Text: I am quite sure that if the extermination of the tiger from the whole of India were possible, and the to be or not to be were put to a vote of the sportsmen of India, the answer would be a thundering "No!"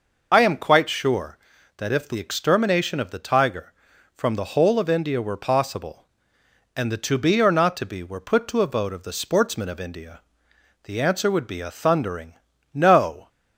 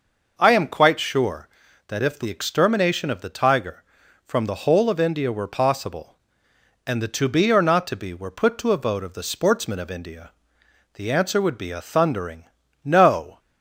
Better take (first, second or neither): second